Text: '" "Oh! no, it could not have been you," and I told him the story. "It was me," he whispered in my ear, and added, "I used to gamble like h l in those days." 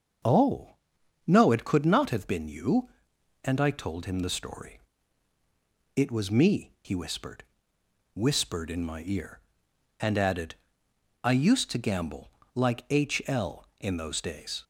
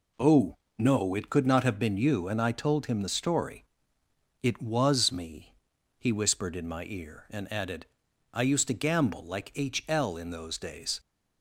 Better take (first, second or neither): second